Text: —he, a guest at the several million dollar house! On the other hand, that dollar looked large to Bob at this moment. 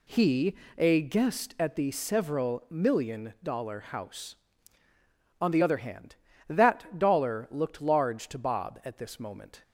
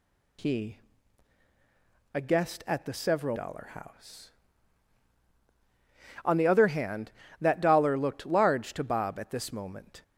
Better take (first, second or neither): first